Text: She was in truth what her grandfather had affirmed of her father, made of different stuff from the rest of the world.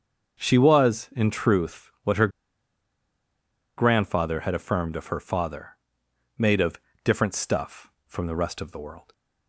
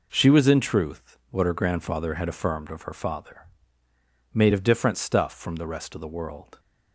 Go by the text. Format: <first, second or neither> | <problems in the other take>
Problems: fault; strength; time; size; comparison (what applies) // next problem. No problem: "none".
second | starts louder than the rest; until 1.4 s; 6.5 dB // pauses between "her" and "grandfather"; strong; at 2.2 s; 1.4 s long // pauses between "of" and "different"; slight; at 6.8 s; 0.24 s long